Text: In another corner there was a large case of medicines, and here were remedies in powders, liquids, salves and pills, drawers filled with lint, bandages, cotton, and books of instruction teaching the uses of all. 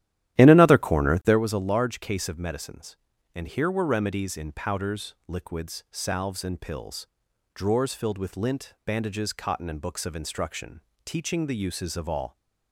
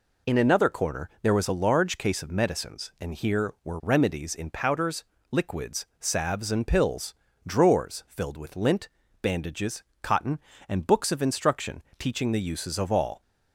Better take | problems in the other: second | starts louder than the rest; strong; until 1.4 s; 13 dB // pauses between "instruction" and "teaching"; slight; at 10.8 s; 0.24 s long; slight in the second

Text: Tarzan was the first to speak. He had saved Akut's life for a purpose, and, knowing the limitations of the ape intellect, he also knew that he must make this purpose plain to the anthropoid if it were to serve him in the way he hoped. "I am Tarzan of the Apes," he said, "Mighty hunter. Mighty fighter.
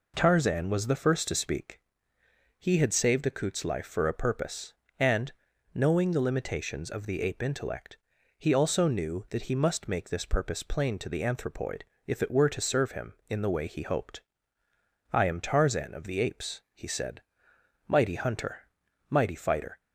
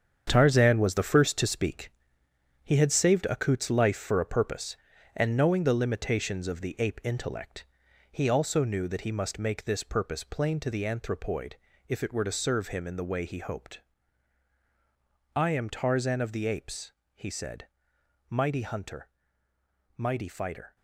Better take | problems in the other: first | gets quieter; strong; throughout; 9.5 dB // pauses between "anthropoid" and "if"; slight; at 11.5 s; 0.32 s long; slight in the first

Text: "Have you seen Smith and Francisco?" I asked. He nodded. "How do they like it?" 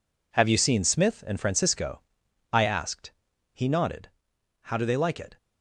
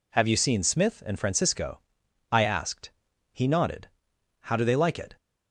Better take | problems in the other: second | gets quieter; strong; throughout; 11.5 dB

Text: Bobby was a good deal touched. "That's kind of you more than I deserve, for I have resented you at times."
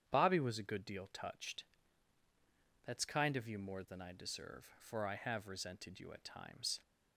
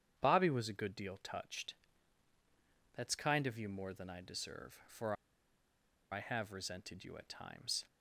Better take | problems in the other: first | starts louder than the rest; strong; until 1.1 s; 9 dB; strong in the first // pauses between "for" and "I"; at 5.1 s; 0.98 s long

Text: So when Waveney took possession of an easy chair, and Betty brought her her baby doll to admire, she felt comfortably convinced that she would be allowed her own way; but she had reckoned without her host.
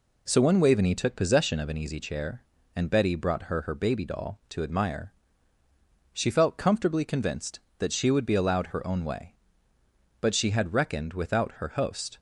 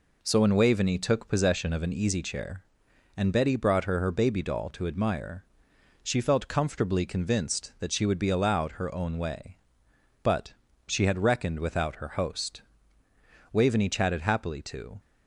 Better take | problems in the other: first | pauses between "but" and "she"; slight; at 10.5 s; 0.34 s long // goes on to say "Waveney chatted happily to"; from 13.5 s on; 1.4 s long

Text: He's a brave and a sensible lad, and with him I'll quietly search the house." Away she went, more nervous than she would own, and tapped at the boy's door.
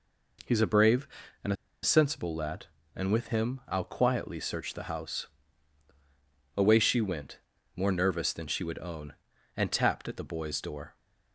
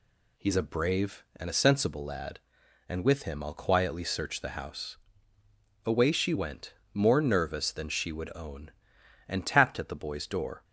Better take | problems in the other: second | pauses between "a" and "sensible"; slight; at 1.5 s; 0.29 s long

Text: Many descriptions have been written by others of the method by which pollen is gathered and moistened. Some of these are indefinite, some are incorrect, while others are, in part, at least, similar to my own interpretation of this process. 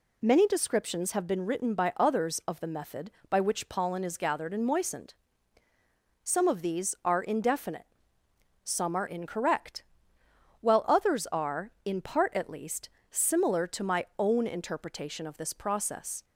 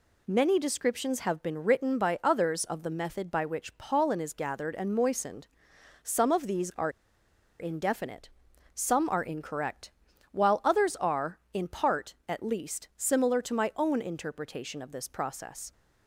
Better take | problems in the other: first | pauses between "are" and "indefinite"; noticeable; at 6.8 s; 0.70 s long

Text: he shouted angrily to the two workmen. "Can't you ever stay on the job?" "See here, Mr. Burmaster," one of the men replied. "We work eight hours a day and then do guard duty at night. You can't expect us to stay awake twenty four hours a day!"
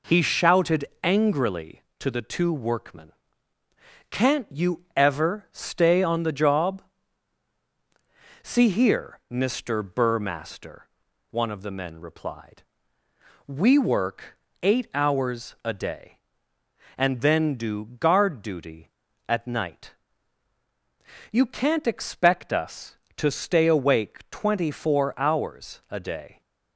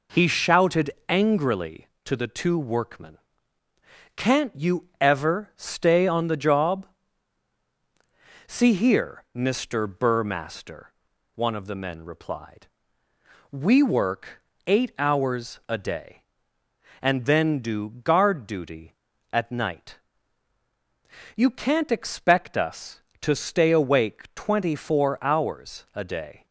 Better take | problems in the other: neither | pauses between "shouted" and "angrily"; slight; the same in both // pauses between "work" and "eight"; slight; the same in both

